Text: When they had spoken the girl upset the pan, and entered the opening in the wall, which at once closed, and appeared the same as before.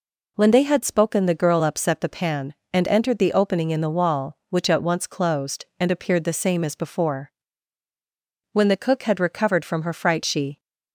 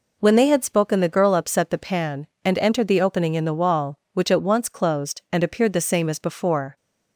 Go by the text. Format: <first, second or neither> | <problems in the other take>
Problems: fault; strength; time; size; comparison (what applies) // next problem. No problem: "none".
second | goes on to say "When the cook had recovered from her fright she"; strong; from 8.5 s on; 2.0 s long